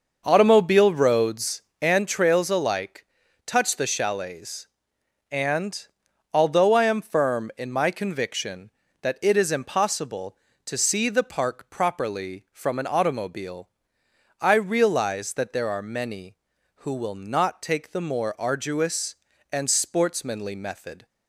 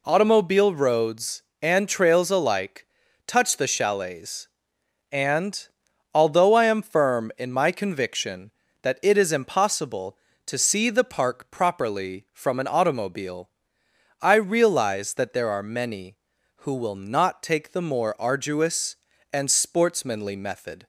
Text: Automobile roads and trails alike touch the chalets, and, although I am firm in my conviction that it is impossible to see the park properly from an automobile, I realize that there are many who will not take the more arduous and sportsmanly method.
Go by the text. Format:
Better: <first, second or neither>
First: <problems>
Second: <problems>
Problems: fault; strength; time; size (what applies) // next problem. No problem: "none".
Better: second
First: starts louder than the rest; noticeable; until 2.1 s; 6 dB // pauses between "alike" and "touch"; at 3.0 s; 0.40 s long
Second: pauses between "alike" and "touch"; at 2.8 s; 0.40 s long